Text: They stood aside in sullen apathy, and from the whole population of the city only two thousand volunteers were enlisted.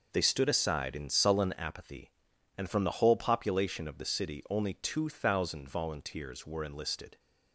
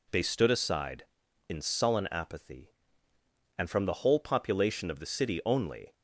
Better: first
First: none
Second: stops before "two thousand volunteers were enlisted"; at 5.9 s

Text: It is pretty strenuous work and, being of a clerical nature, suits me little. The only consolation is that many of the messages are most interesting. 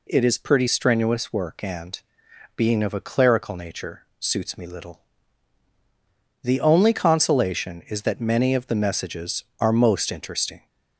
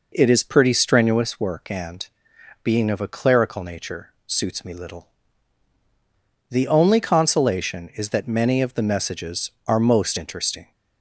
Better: first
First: none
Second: starts louder than the rest; noticeable; until 1.3 s; 4.5 dB

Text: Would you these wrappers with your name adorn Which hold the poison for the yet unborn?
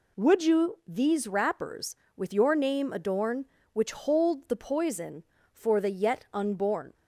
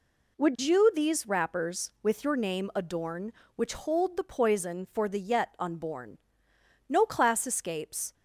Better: first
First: none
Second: goes on to say "No class escapes"; noticeable; from 6.8 s on; 1.2 s long

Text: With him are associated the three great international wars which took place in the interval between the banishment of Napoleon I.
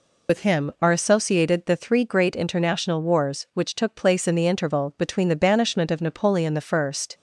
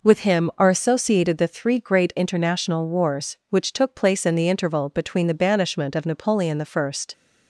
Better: second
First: loses the start of "With"; at 0.2 s; 65 ms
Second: none

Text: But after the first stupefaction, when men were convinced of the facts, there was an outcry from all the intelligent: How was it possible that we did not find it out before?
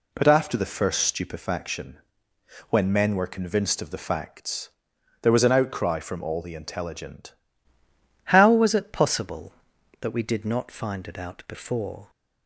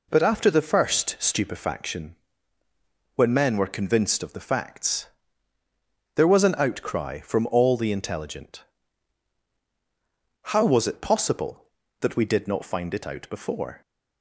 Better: second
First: changes voice at "How"; from 8.2 s on; 3.8 s long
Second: none

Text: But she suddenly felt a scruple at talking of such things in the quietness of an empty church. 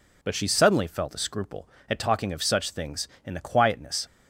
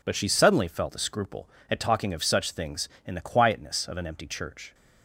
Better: second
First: stops before "of an empty church"; at 4.0 s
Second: none

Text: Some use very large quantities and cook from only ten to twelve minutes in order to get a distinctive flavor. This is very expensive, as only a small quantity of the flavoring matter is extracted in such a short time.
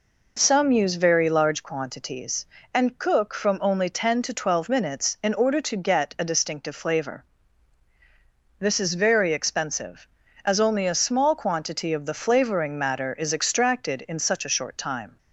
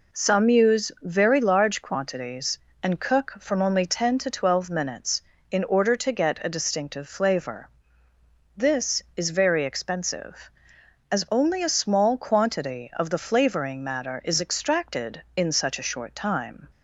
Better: neither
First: none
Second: none

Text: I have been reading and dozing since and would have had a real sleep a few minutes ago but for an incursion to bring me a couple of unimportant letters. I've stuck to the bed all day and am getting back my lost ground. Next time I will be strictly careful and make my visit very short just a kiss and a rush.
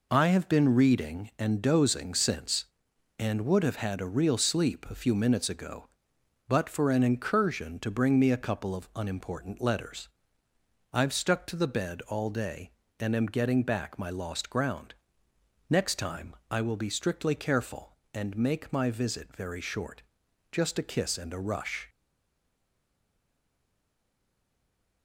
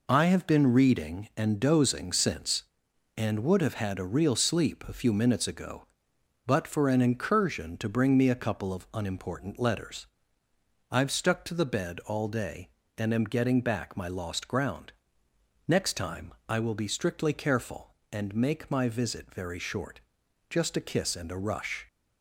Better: second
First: pauses between "short" and "just"; noticeable; at 20.0 s; 0.50 s long // stays silent after the last word; strong; from 21.8 s on; 3.2 s long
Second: pauses between "short" and "just"; noticeable; at 20.0 s; 0.50 s long

